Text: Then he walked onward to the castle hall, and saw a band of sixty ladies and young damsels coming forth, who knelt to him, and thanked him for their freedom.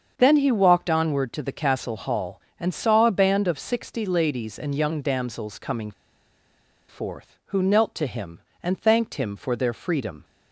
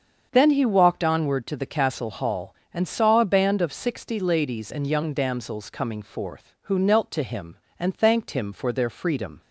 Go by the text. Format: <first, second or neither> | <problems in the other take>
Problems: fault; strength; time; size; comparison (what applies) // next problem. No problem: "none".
second | starts louder than the rest; until 1.1 s; 7 dB; also in the second // pauses between "coming" and "forth"; noticeable; at 5.9 s; 0.97 s long